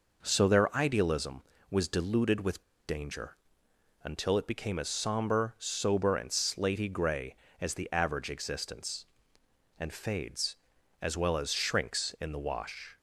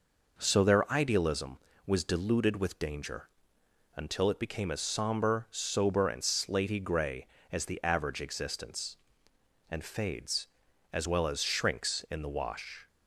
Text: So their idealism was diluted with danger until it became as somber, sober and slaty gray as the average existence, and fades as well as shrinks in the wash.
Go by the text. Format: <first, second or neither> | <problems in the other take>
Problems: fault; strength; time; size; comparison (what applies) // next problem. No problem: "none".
second | pauses between "with" and "danger"; slight; at 2.6 s; 0.24 s long // pauses between "danger" and "until"; noticeable; at 3.3 s; 0.66 s long; noticeable in the second